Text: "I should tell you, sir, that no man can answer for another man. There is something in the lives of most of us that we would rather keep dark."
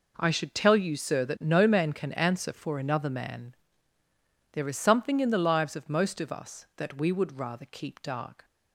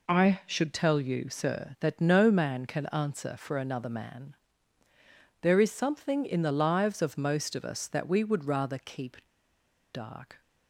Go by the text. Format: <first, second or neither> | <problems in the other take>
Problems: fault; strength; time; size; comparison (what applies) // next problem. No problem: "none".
first | pauses between "keep" and "dark"; noticeable; at 9.2 s; 0.69 s long